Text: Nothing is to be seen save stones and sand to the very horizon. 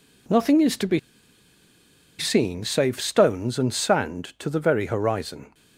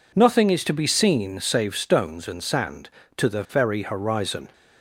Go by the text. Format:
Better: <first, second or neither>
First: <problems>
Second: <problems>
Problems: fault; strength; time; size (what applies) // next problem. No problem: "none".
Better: second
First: pauses between "be" and "seen"; at 0.9 s; 1.1 s long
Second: none